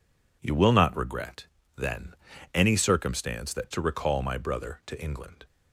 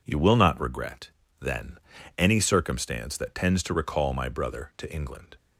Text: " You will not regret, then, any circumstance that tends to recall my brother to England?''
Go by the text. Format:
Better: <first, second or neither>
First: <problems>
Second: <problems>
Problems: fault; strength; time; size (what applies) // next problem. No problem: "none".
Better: second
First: skips "tends"; at 3.7 s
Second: none